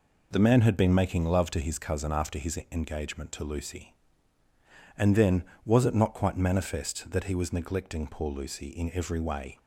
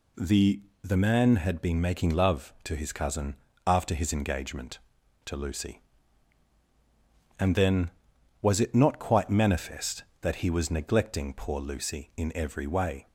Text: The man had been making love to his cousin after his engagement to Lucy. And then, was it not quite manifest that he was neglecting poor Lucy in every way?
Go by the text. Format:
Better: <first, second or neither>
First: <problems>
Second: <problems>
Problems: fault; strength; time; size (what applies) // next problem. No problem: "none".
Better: first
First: none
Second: says "The" twice; at 0.8 s // pauses between "cousin" and "after"; slight; at 3.3 s; 0.32 s long